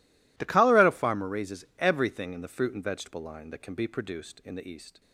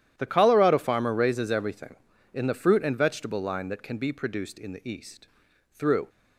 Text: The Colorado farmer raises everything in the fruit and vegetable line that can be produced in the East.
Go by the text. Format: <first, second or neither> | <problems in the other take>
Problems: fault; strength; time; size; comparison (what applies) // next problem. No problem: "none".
first | starts louder than the rest; strong; until 1.1 s; 11.5 dB // goes on to say "Through"; slight; from 5.7 s on; 0.36 s long